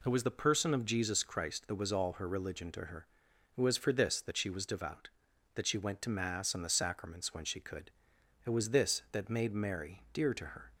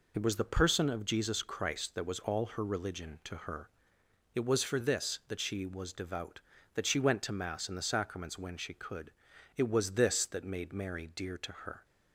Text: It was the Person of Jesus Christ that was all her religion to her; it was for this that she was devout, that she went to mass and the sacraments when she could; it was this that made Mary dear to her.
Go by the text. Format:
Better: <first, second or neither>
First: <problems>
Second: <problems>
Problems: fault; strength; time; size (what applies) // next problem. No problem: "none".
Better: first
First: none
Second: loses the start of "It"; at 0.1 s; 30 ms